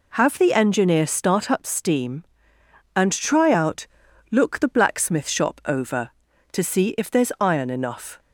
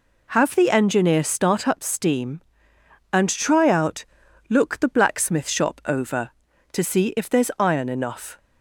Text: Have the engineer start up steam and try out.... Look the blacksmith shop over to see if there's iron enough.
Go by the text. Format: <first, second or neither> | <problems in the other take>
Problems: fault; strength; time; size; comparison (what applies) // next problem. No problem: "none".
neither | none